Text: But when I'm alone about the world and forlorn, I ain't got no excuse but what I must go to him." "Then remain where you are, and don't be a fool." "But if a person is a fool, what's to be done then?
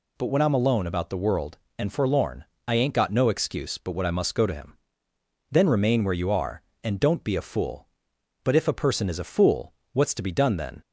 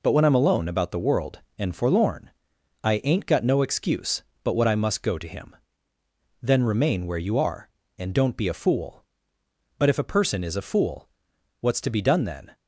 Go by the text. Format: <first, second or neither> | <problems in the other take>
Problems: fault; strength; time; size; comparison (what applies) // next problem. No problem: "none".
neither | none